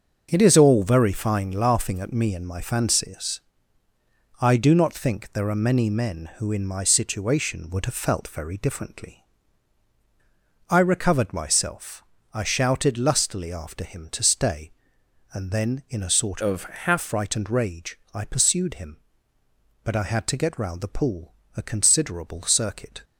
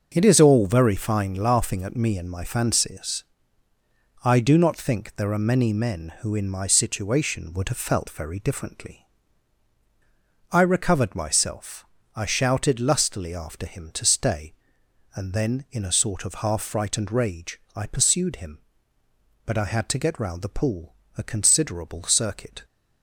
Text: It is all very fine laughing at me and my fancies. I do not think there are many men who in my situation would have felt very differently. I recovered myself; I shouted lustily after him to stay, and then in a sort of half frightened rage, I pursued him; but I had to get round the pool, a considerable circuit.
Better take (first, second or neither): second